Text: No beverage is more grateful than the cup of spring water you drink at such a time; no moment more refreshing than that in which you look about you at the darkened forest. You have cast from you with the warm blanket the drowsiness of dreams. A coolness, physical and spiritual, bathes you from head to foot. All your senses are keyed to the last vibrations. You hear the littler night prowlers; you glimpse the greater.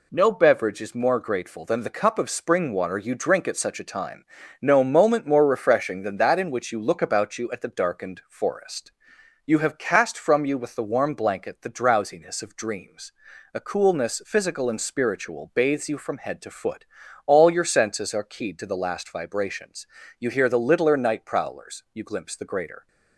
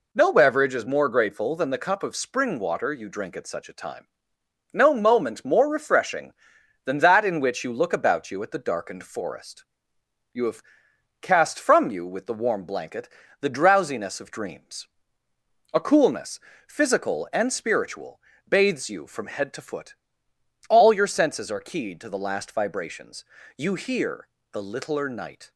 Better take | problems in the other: first | pauses between "have" and "cast"; noticeable; at 10.6 s; 0.60 s long // pauses between "blanket" and "the"; slight; at 13.0 s; 0.32 s long // pauses between "hear" and "the"; slight; at 24.2 s; 0.24 s long // stops before "prowlers you glimpse the greater"; at 25.5 s

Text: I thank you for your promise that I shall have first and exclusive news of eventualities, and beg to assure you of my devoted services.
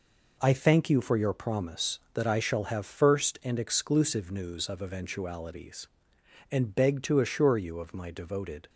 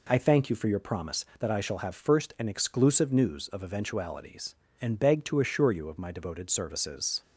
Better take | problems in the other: second | stops before "services"; at 8.6 s

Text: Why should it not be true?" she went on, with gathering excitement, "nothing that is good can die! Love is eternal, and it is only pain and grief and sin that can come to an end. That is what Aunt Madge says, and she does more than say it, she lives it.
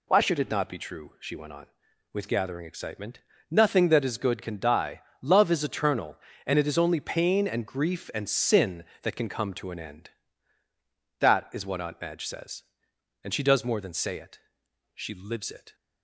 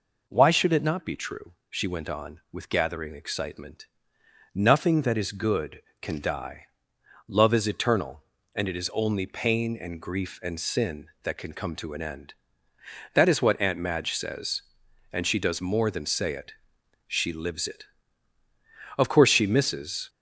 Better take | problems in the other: first | goes on to say "Of course she misses"; noticeable; from 18.9 s on; 1.1 s long

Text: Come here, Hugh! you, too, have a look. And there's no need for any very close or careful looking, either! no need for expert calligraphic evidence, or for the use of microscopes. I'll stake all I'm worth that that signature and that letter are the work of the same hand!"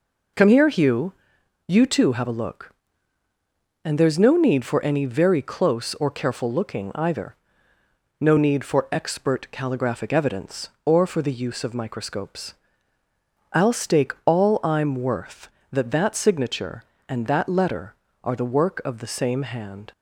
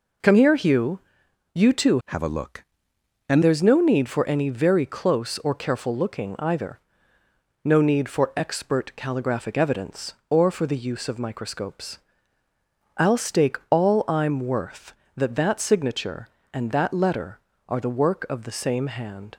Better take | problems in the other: first | changes voice from "have" to "And"; from 2.0 to 3.4 s; 1.4 s long

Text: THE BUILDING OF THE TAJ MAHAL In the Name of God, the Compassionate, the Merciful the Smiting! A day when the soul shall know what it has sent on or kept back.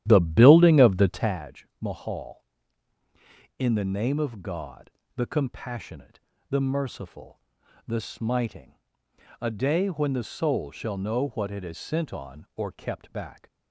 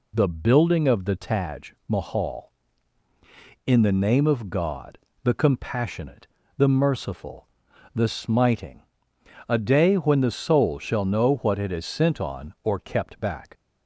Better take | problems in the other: second | starts louder than the rest; strong; until 1.5 s; 12 dB // pauses between "TAJ" and "MAHAL"; slight; at 1.6 s; 0.16 s long; slight in the second // pauses between "Merciful" and "the"; noticeable; at 7.4 s; 0.48 s long; noticeable in the second

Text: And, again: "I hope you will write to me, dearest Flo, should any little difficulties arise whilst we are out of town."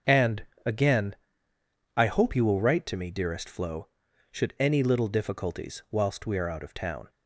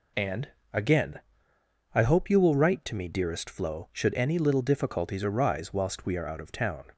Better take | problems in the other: second | starts louder than the rest; until 2.0 s; 7 dB // skips "arise"; at 5.8 s

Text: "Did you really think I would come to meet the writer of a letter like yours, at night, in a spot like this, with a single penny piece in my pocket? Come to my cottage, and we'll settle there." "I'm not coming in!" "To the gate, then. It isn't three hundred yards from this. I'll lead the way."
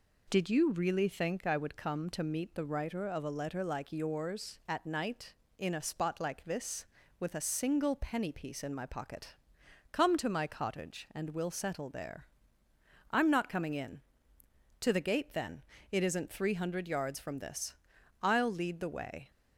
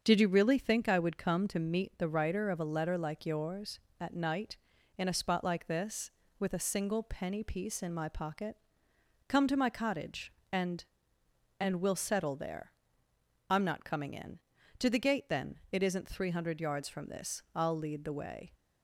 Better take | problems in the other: first | starts louder than the rest; until 1.0 s; 6.5 dB // says "and" twice; at 11.5 s

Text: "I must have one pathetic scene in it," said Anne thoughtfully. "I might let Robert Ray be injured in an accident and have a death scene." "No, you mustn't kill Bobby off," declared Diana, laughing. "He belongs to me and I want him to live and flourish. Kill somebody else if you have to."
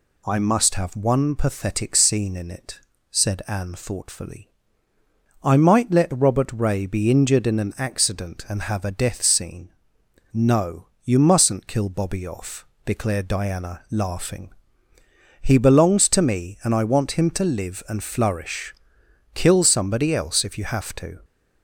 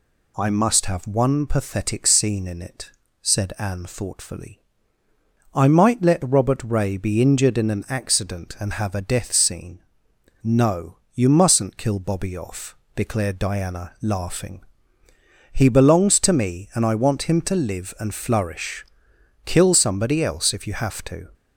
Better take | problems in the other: neither | none

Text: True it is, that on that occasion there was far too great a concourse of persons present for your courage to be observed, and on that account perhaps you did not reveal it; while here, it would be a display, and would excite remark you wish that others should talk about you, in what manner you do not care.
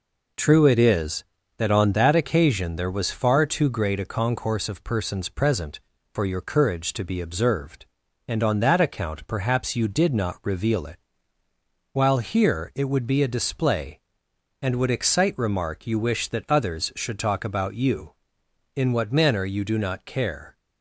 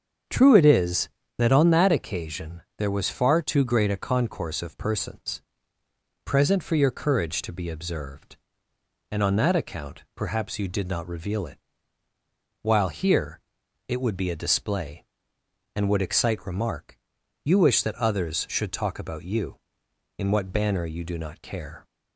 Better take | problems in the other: first | starts louder than the rest; strong; until 1.5 s; 7 dB // pauses between "occasion" and "there"; slight; at 2.6 s; 0.16 s long // pauses between "persons" and "present"; noticeable; at 5.4 s; 0.82 s long // pauses between "remark" and "you"; noticeable; at 16.9 s; 0.48 s long // says "banner" for "manner"; at 20.5 s

